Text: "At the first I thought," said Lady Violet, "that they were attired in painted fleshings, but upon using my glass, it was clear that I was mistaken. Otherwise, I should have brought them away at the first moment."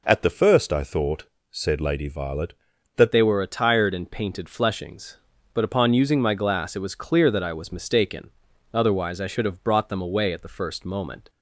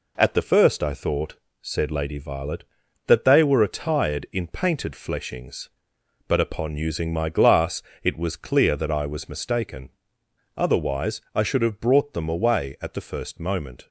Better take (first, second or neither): second